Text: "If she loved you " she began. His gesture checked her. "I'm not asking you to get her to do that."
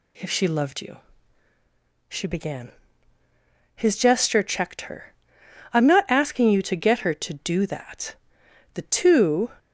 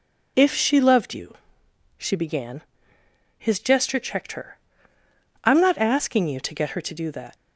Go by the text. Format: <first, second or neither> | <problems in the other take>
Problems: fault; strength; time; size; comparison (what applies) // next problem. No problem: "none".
second | goes on to say "The two"; noticeable; from 8.7 s on; 0.78 s long